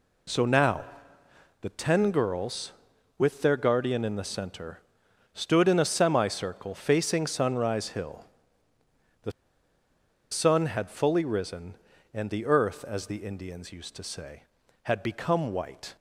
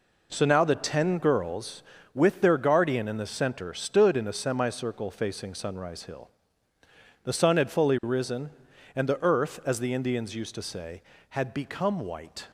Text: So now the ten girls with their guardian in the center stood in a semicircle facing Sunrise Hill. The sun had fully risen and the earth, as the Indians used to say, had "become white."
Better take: second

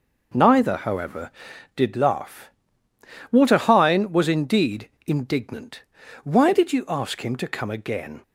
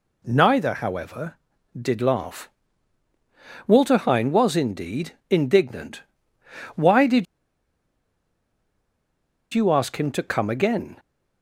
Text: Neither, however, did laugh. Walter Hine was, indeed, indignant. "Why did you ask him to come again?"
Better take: first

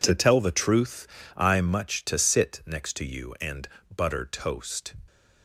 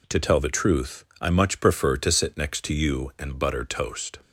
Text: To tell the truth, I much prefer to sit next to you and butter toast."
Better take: second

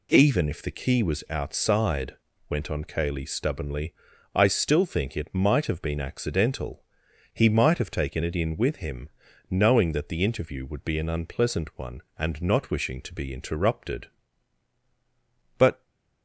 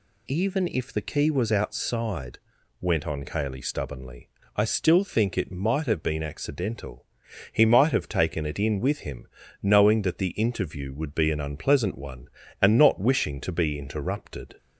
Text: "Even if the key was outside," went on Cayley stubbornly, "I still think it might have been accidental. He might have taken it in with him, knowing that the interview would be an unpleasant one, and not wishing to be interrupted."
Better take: second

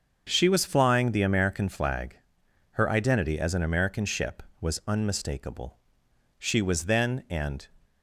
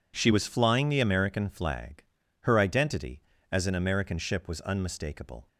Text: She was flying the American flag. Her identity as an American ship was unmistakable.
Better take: second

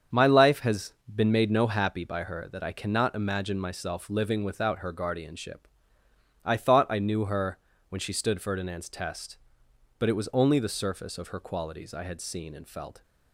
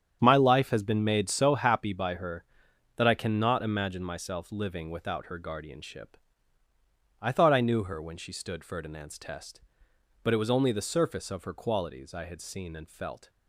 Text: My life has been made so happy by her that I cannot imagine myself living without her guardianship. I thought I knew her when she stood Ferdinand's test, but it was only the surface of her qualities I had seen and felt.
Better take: second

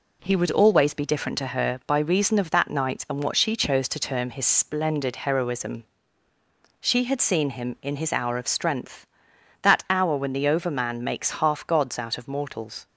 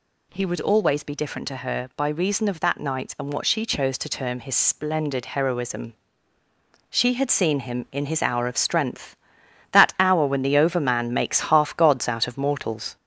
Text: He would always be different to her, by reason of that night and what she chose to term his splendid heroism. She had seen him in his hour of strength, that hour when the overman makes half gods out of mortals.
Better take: first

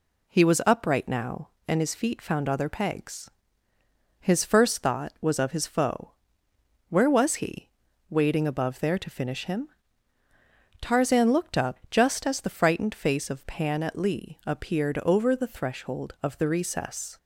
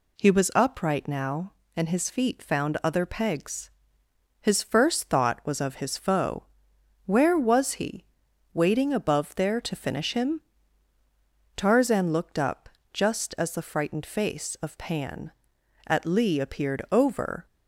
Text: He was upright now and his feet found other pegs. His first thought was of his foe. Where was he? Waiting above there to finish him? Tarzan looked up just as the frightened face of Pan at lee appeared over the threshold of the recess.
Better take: first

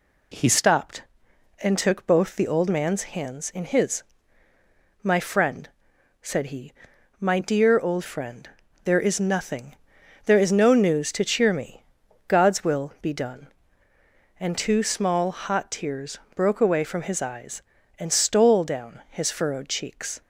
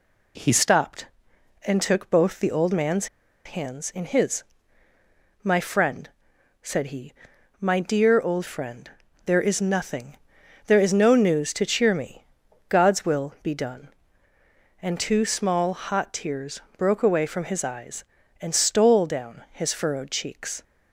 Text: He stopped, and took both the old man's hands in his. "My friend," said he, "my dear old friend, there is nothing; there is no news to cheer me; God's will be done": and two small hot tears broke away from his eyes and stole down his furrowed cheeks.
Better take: first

